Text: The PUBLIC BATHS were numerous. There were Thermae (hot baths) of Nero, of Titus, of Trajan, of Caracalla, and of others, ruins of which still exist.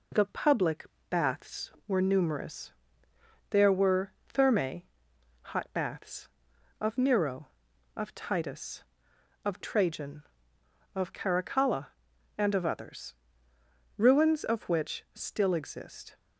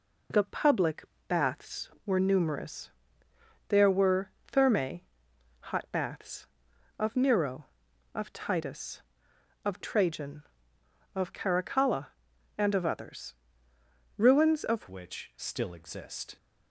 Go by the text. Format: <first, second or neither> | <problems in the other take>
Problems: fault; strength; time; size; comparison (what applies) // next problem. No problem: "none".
first | pauses between "PUBLIC" and "BATHS"; slight; at 1.0 s; 0.24 s long; slight in the first // pauses between "were" and "Thermae"; slight; at 4.2 s; 0.16 s long; slight in the first // changes voice at "which"; from 14.9 s on; 1.4 s long